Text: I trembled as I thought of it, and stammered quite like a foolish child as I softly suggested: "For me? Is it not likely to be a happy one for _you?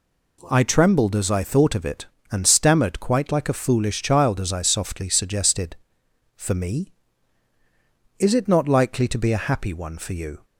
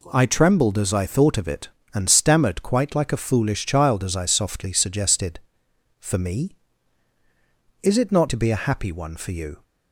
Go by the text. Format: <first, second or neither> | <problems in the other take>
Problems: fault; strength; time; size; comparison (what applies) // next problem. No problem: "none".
first | skips "likely"; at 8.2 s